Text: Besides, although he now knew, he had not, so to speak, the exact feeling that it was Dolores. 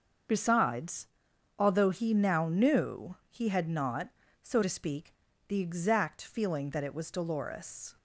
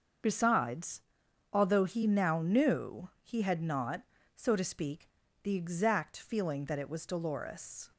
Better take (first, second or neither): neither